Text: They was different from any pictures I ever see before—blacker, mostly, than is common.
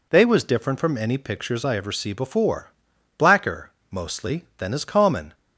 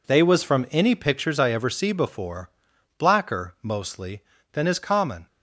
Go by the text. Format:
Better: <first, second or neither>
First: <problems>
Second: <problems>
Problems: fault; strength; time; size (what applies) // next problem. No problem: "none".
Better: first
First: none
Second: skips "different"; at 0.4 s